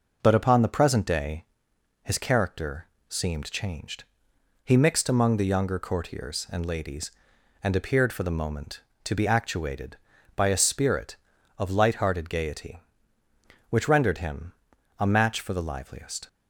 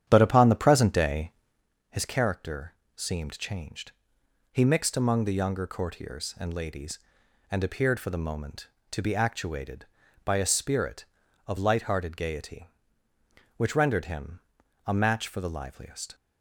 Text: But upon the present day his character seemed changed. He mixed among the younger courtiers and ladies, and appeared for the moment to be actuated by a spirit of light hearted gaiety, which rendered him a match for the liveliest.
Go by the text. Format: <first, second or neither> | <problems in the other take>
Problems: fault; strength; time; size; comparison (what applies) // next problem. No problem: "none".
first | starts louder than the rest; strong; until 1.7 s; 9.5 dB // pauses between "day" and "his"; noticeable; at 1.3 s; 0.58 s long; noticeable in the first // pauses between "character" and "seemed"; slight; at 2.7 s; 0.22 s long; slight in the first // pauses between "him" and "a"; noticeable; at 14.4 s; 0.46 s long; noticeable in the first